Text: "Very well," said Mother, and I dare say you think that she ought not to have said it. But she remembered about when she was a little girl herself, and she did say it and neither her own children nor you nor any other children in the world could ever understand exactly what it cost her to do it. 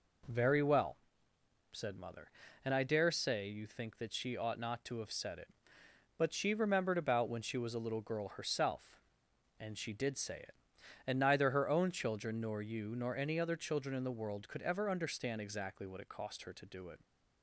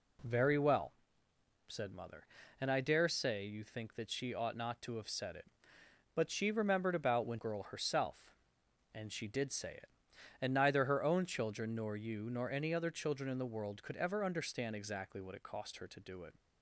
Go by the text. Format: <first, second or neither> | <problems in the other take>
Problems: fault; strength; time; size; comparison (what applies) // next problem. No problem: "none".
first | skips "she was a little"; at 7.3 s